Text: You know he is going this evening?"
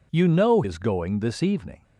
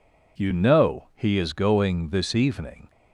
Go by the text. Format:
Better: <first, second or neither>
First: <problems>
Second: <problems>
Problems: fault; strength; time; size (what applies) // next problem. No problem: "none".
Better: second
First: skips "he"; at 0.6 s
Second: none